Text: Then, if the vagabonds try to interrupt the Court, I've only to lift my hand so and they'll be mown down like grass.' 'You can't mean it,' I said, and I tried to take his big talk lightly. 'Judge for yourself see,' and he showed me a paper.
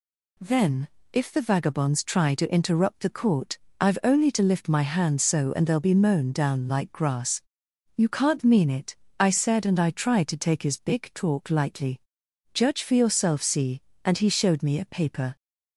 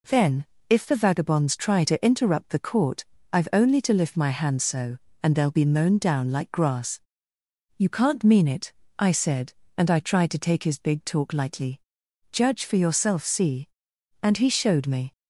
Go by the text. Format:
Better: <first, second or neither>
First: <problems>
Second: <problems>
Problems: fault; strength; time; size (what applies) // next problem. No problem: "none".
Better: first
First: none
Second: stops before "a paper"; at 15.1 s